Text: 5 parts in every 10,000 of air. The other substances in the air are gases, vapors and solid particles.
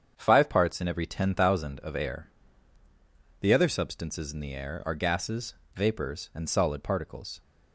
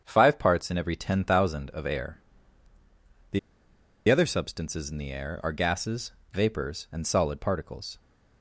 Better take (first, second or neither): first